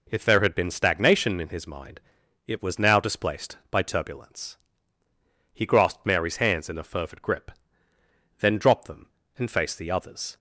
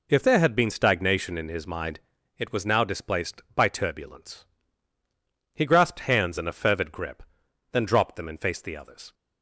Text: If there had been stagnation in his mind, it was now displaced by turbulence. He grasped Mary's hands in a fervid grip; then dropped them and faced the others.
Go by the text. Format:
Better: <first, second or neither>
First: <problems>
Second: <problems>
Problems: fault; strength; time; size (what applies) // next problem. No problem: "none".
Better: first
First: none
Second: skips "Mary's"; at 6.0 s